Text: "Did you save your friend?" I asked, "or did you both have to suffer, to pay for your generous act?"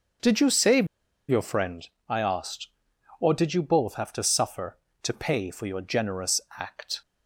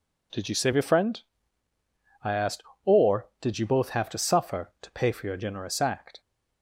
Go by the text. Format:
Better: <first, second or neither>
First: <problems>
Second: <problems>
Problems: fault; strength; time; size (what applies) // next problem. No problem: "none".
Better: second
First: starts louder than the rest; noticeable; until 1.6 s; 6 dB // pauses between "save" and "your"; at 0.8 s; 0.42 s long // pauses between "generous" and "act"; slight; at 6.3 s; 0.20 s long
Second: none